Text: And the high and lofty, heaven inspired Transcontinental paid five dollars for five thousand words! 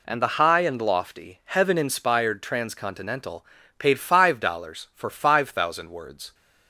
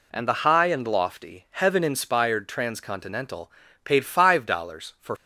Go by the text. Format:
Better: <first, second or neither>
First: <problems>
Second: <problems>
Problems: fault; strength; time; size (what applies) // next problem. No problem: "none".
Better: first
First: pauses between "Transcontinental" and "paid"; slight; at 3.4 s; 0.32 s long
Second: pauses between "Transcontinental" and "paid"; slight; at 3.5 s; 0.32 s long // stops before "five thousand words"; at 5.1 s